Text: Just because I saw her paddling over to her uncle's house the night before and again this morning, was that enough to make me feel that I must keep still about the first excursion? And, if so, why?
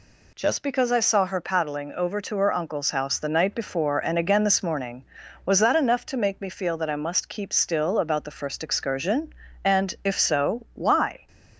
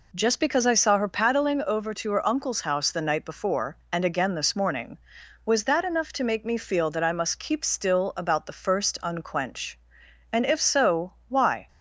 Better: first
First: none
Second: says "unquench" for "excursion"; at 9.0 s

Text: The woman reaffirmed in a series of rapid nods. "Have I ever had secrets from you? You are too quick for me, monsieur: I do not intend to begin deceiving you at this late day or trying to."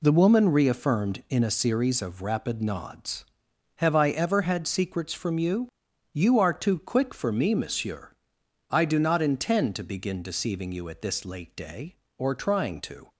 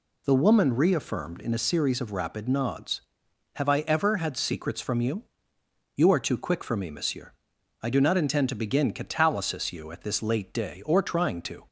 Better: first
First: none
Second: says "catalysis" for "deceiving"; at 8.9 s

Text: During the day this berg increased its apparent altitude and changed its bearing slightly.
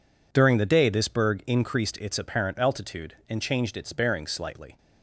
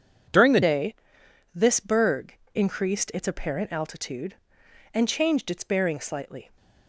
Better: first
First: none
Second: changes voice at "day"; from 0.6 s on; 5.9 s long // pauses between "day" and "this"; noticeable; at 0.9 s; 0.58 s long // pauses between "berg" and "increased"; slight; at 2.3 s; 0.18 s long

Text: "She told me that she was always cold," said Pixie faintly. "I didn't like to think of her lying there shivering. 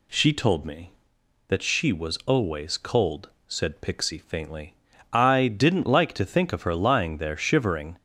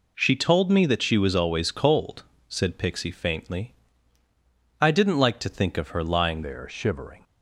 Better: first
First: none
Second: changes voice at "there"; from 6.4 s on; 0.8 s long

